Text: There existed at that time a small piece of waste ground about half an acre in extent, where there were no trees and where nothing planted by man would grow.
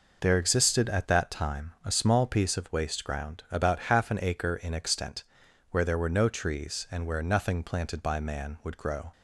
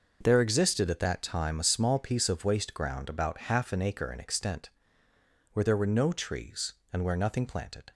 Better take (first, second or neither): first